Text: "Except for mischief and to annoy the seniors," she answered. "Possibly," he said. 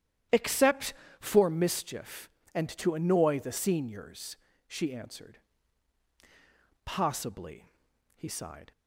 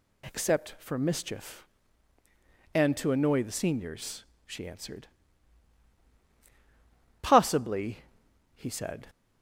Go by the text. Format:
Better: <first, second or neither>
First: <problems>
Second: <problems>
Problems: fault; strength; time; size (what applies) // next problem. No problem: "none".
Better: second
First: starts louder than the rest; strong; until 1.5 s; 10.5 dB // says "sighed" for "said"; at 8.2 s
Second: none